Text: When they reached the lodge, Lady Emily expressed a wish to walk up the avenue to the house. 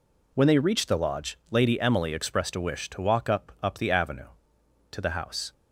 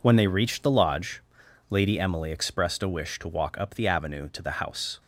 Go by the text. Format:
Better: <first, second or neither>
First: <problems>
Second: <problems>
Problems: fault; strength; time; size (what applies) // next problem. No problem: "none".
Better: second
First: says "up" twice; at 3.6 s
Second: none